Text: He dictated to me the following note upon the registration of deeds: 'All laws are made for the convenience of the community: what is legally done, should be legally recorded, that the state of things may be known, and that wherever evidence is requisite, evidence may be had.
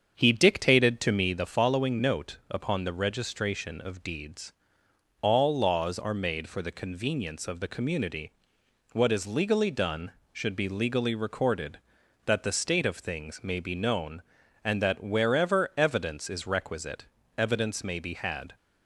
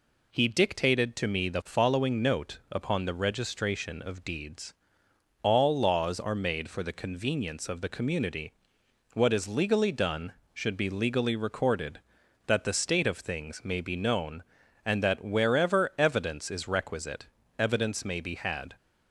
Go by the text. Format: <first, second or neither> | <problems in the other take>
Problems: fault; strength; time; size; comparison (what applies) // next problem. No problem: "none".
second | starts louder than the rest; strong; until 1.4 s; 7.5 dB